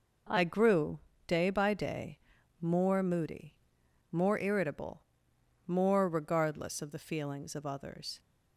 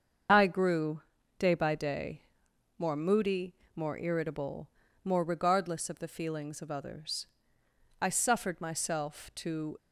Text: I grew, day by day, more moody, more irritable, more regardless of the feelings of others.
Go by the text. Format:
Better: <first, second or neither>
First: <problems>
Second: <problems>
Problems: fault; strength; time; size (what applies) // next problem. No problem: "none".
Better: first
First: none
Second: starts louder than the rest; until 1.6 s; 7 dB // goes on to say "I suffered myself to"; strong; from 7.9 s on; 1.7 s long